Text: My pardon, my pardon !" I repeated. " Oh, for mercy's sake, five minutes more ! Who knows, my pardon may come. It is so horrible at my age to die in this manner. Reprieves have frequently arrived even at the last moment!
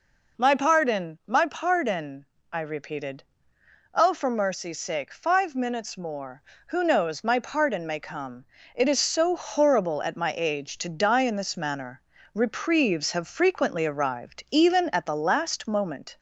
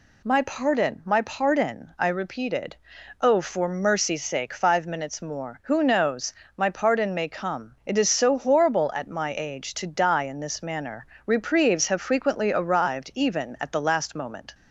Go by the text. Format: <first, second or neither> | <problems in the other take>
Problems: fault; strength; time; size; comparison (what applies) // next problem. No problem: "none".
neither | none